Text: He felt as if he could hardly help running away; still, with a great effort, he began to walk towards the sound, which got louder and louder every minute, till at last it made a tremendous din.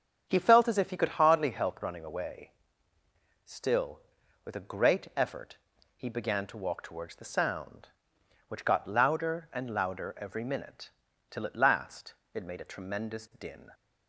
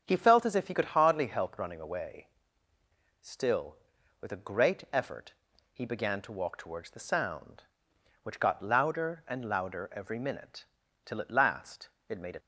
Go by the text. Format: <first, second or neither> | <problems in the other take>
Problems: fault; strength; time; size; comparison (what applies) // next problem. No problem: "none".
first | starts louder than the rest; strong; until 1.0 s; 7.5 dB; strong in the first // pauses between "last" and "it"; slight; at 11.8 s; 0.20 s long; slight in the first // stops before "tremendous din"; at 12.3 s